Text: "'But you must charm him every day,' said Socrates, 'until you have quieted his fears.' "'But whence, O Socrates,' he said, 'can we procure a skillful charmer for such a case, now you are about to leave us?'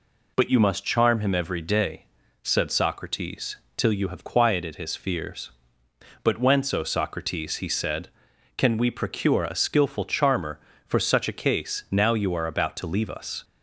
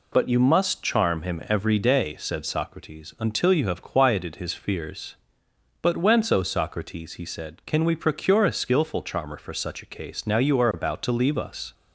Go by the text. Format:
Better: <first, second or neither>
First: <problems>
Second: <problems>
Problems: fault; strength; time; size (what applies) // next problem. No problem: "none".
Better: second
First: says "till" for "until"; at 3.7 s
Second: none